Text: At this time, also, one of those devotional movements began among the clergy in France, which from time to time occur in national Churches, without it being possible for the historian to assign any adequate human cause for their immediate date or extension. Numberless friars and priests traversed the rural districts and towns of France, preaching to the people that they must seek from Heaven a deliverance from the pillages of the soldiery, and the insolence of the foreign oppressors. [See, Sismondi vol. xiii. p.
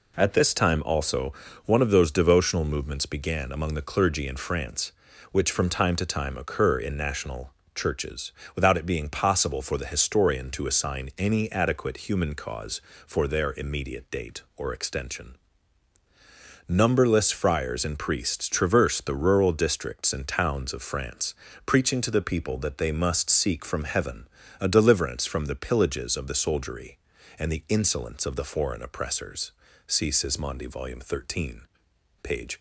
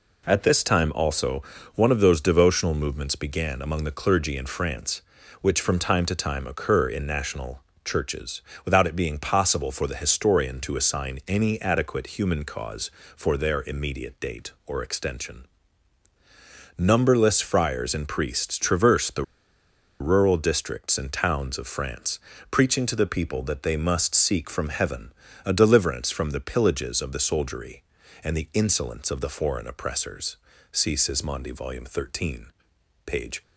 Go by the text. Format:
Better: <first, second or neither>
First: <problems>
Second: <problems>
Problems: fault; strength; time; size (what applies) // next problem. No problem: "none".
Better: first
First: pauses between "national" and "Churches"; slight; at 7.5 s; 0.24 s long // pauses between "Heaven" and "a"; slight; at 24.2 s; 0.32 s long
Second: pauses between "national" and "Churches"; slight; at 7.6 s; 0.24 s long // pauses between "the" and "rural"; noticeable; at 19.2 s; 0.75 s long // pauses between "Heaven" and "a"; slight; at 25.1 s; 0.32 s long